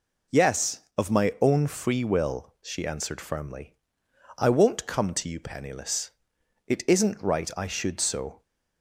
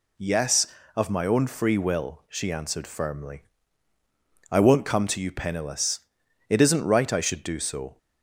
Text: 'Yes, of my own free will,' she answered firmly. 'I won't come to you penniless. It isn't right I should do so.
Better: second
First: skips "do"; at 7.9 s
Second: none

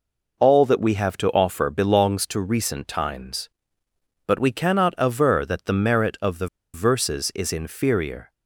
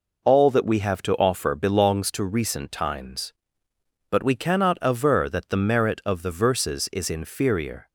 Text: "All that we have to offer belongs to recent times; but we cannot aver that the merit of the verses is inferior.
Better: second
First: pauses between "the" and "verses"; slight; at 6.4 s; 0.28 s long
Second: none

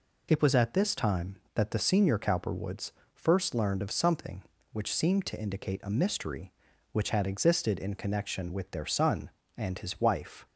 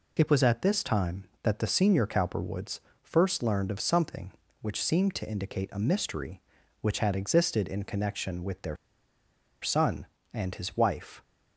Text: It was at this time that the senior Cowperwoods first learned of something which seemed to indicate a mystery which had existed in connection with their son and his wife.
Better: first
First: pauses between "Cowperwoods" and "first"; slight; at 2.9 s; 0.24 s long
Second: pauses between "Cowperwoods" and "first"; slight; at 2.7 s; 0.24 s long // pauses between "their" and "son"; noticeable; at 8.7 s; 0.86 s long

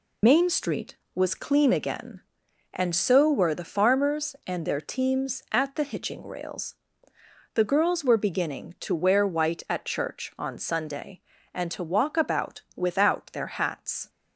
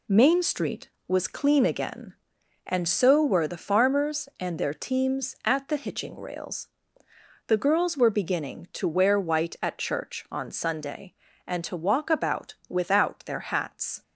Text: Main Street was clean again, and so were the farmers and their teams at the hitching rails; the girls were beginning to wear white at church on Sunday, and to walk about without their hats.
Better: second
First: loses the start of "Main"; at 0.2 s; 80 ms // pauses between "about" and "without"; slight; at 12.5 s; 0.16 s long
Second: pauses between "about" and "without"; slight; at 12.5 s; 0.16 s long

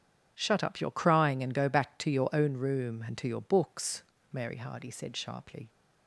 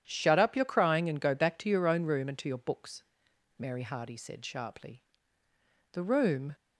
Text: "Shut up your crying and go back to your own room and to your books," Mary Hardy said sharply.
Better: first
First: none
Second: goes on to say "The room"; from 5.9 s on; 0.60 s long

